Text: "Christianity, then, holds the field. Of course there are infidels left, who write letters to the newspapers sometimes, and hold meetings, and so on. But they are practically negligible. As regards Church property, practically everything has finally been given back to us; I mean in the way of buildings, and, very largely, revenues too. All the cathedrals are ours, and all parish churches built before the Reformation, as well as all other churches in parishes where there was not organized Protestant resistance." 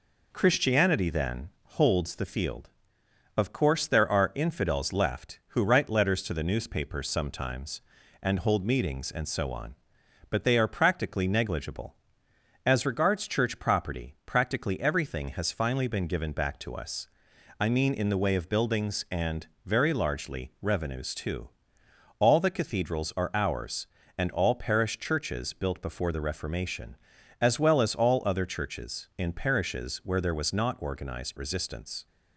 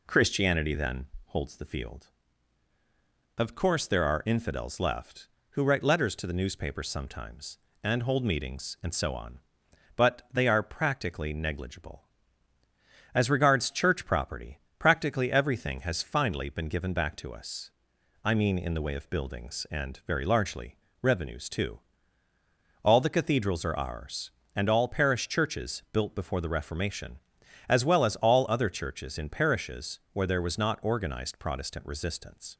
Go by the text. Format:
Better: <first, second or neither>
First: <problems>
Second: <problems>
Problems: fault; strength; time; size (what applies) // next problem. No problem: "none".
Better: second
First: skips "Protestant"; at 31.3 s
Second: none